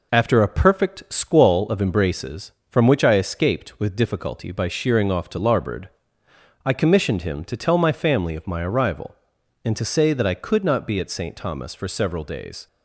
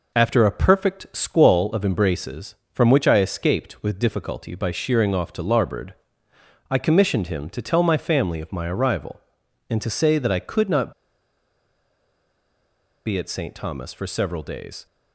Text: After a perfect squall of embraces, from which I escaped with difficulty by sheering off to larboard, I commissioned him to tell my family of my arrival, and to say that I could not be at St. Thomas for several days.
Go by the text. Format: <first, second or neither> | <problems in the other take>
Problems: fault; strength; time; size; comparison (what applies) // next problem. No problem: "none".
first | pauses between "not" and "be"; strong; at 10.9 s; 2.1 s long